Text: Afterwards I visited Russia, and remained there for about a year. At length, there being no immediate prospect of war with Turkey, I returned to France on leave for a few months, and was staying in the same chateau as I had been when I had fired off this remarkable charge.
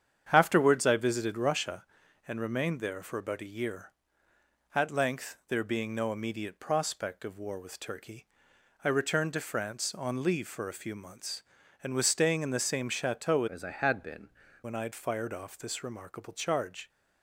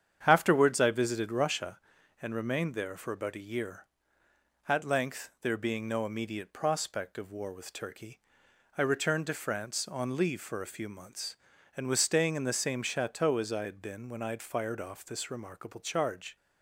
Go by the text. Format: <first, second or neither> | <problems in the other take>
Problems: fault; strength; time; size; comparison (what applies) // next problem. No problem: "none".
second | starts louder than the rest; strong; until 1.3 s; 8.5 dB; strong in the second // changes voice from "as" to "been"; from 13.4 to 14.2 s; 0.8 s long